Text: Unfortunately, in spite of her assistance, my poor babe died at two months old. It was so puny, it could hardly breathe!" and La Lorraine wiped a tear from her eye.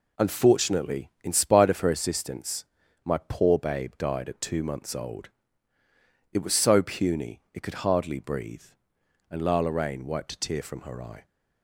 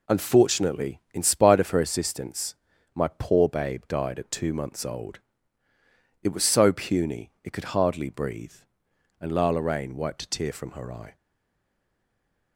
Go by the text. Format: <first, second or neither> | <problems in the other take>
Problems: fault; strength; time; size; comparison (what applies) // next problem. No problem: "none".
first | stays silent after the last word; noticeable; from 11.1 s on; 1.4 s long